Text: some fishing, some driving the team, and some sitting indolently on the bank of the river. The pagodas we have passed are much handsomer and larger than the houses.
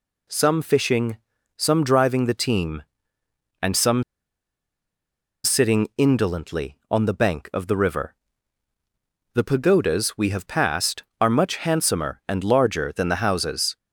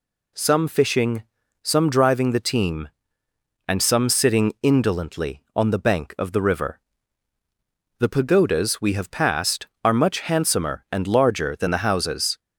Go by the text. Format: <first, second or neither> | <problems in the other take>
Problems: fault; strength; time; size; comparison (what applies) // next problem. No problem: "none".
second | pauses between "some" and "sitting"; strong; at 4.0 s; 1.4 s long